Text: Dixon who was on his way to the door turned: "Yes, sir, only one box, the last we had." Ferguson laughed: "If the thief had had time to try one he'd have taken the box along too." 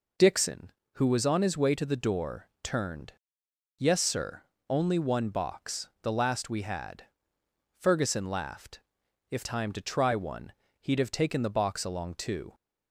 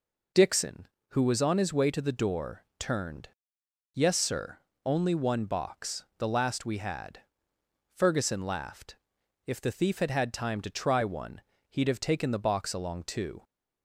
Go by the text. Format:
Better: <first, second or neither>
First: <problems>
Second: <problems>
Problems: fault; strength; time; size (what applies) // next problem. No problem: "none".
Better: second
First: skips "the thief had had"; at 9.4 s // pauses between "one" and "he'd"; slight; at 10.5 s; 0.30 s long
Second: pauses between "one" and "he'd"; slight; at 11.3 s; 0.30 s long